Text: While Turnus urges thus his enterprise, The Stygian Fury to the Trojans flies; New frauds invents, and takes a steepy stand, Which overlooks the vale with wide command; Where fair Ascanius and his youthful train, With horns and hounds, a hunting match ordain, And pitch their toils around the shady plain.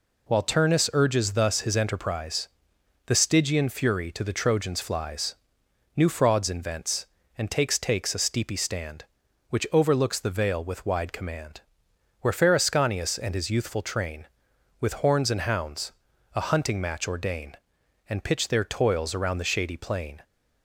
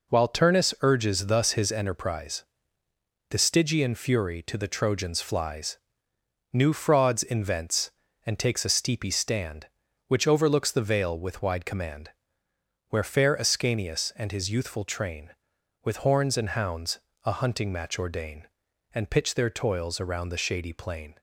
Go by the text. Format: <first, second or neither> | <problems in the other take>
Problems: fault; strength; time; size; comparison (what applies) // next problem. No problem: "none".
second | says "takes" twice; at 7.7 s